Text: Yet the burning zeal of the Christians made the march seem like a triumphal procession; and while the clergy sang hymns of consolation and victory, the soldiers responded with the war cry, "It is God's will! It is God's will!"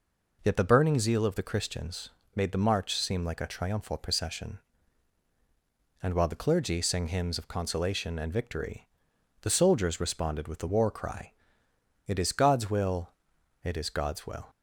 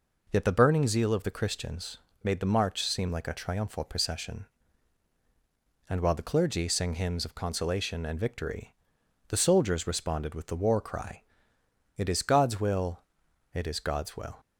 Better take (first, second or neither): neither